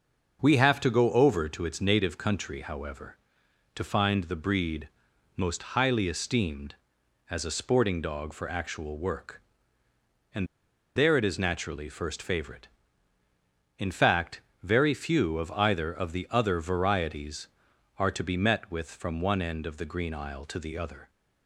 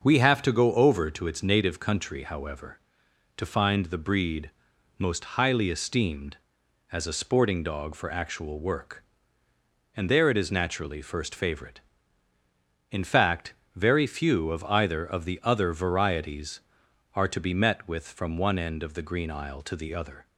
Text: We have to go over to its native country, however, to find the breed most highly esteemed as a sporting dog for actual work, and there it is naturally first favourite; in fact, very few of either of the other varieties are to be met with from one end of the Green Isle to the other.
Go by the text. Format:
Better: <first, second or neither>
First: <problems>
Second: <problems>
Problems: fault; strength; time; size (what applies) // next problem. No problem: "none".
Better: second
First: starts louder than the rest; until 1.4 s; 6.5 dB // pauses between "breed" and "most"; noticeable; at 4.8 s; 0.48 s long // pauses between "and" and "there"; noticeable; at 10.4 s; 0.51 s long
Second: starts louder than the rest; until 1.0 s; 6.5 dB // pauses between "breed" and "most"; noticeable; at 4.5 s; 0.48 s long